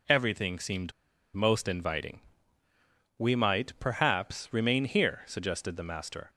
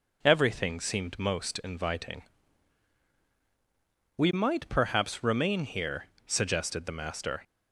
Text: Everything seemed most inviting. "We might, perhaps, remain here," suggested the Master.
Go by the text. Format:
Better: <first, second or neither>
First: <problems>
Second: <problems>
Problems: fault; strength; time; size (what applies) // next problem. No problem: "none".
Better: second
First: pauses between "seemed" and "most"; at 0.9 s; 0.41 s long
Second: none